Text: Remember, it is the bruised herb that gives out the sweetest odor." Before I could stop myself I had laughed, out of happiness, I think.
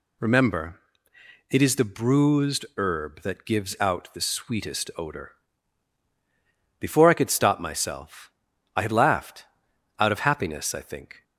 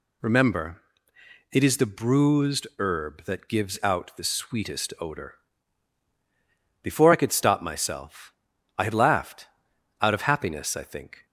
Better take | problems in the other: neither | pauses between "myself" and "I"; the same in both

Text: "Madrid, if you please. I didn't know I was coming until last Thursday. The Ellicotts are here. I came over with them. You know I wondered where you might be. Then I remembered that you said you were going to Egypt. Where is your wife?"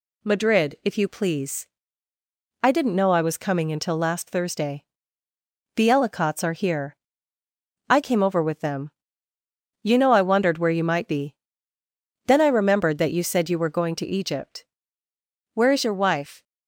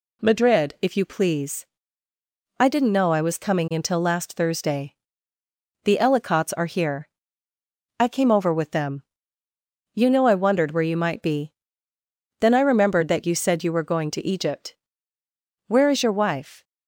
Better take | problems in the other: neither | none

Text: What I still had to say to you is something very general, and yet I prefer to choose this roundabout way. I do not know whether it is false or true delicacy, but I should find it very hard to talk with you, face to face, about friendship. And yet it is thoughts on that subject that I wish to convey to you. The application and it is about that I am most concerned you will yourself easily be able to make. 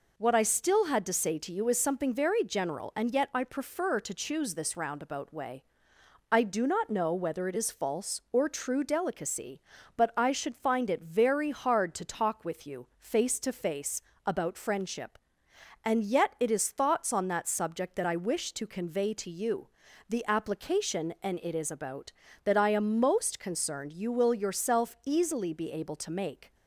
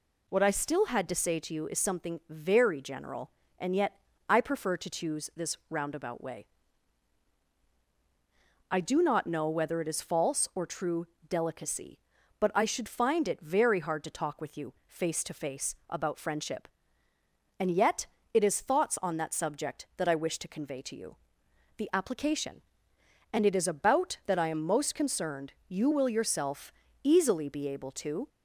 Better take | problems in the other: first | pauses between "yet" and "I"; slight; at 3.9 s; 0.34 s long // pauses between "true" and "delicacy"; slight; at 11.0 s; 0.24 s long // pauses between "yet" and "it"; slight; at 18.0 s; 0.28 s long // pauses between "yourself" and "easily"; slight; at 26.7 s; 0.28 s long // stops before "make"; at 28.2 s

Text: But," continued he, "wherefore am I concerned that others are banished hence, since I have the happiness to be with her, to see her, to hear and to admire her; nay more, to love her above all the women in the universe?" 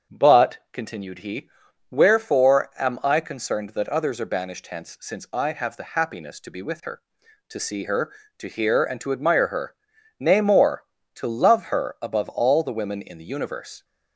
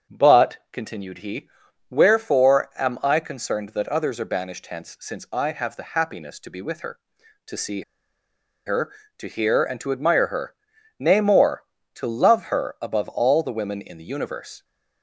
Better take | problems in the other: first | starts louder than the rest; until 1.2 s; 7 dB; also in the first // pauses between "see" and "her"; noticeable; at 7.8 s; 0.84 s long

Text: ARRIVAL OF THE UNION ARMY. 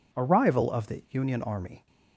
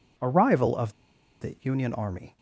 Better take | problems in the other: first | pauses between "OF" and "THE"; noticeable; at 0.9 s; 0.48 s long

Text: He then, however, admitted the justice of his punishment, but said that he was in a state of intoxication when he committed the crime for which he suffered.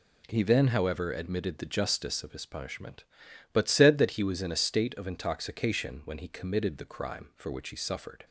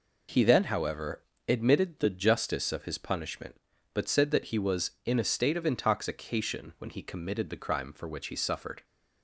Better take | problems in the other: neither | none

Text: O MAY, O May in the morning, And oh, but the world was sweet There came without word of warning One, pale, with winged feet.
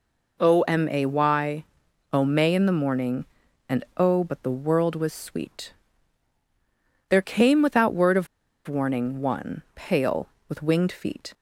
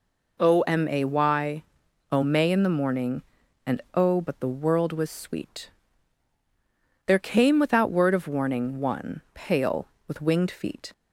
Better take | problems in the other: second | pauses between "sweet" and "There"; strong; at 5.7 s; 1.3 s long; strong in the second // pauses between "of" and "warning"; at 8.2 s; 0.41 s long

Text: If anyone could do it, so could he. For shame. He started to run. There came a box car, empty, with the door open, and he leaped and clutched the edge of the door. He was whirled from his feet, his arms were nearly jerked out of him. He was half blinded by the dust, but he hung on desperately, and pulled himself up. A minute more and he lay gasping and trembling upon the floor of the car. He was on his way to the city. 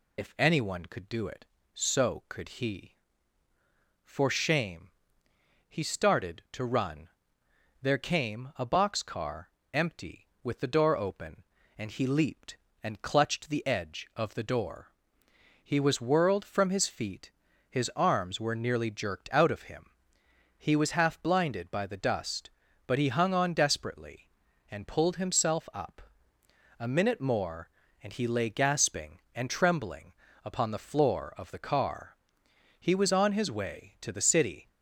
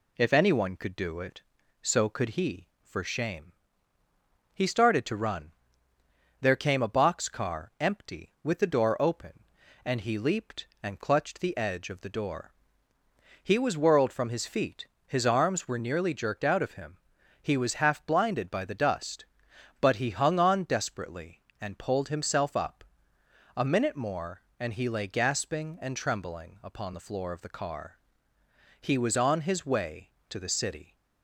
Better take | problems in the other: second | loses the start of "If"; at 0.1 s; 50 ms // pauses between "trembling" and "upon"; slight; at 30.1 s; 0.30 s long

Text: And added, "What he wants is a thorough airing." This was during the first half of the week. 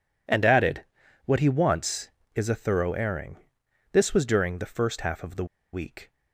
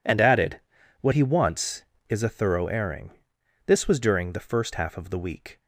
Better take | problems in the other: second | pauses between "the" and "week"; slight; at 5.4 s; 0.28 s long

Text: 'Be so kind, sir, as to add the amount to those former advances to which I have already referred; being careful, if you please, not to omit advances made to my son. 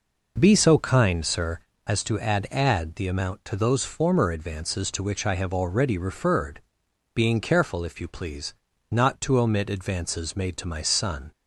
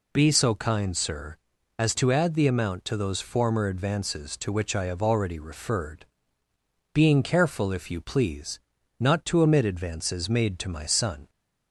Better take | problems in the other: second | says "add" twice; at 2.5 s

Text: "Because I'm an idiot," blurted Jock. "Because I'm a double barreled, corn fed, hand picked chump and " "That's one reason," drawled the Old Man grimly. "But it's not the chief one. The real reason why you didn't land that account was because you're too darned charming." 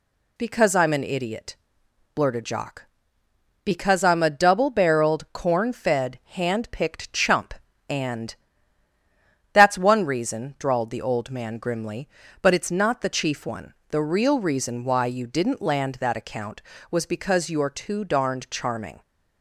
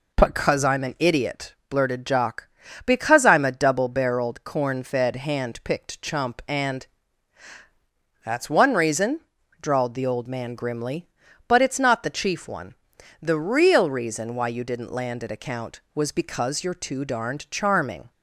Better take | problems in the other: first | says "at" for "that"; at 15.2 s

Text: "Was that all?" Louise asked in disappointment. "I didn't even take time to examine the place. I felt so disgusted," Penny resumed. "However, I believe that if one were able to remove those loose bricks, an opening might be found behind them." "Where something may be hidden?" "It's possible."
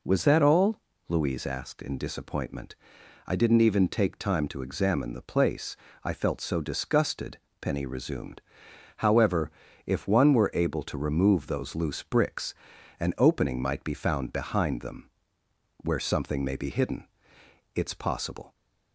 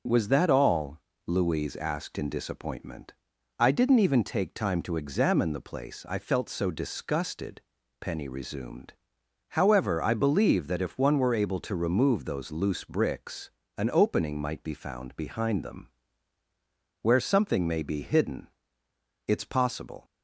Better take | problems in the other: second | skips "I believe that"; at 9.6 s

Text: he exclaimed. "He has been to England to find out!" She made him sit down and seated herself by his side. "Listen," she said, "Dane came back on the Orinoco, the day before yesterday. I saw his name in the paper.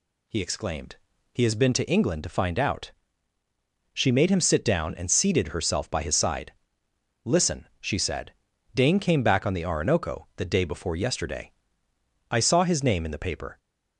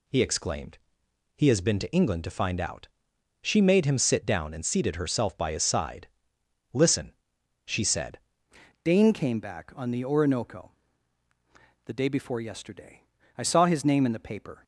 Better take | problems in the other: first | changes voice at "Dane"; from 8.8 s on; 5.8 s long

